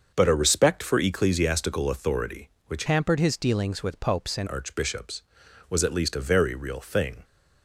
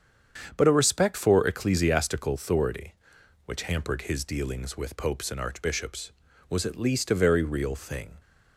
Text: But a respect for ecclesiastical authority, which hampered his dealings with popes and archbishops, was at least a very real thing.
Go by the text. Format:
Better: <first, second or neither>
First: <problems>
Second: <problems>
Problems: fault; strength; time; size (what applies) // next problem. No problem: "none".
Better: second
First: starts louder than the rest; until 1.1 s; 6.5 dB // changes voice from "hampered" to "and"; from 2.8 to 4.4 s; 1.6 s long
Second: starts louder than the rest; strong; until 1.5 s; 7.5 dB